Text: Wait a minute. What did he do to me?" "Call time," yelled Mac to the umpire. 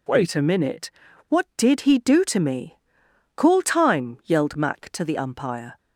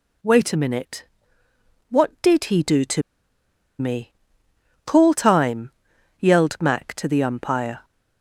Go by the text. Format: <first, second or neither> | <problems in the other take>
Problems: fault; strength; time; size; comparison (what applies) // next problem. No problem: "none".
first | pauses between "to" and "me"; noticeable; at 3.0 s; 0.77 s long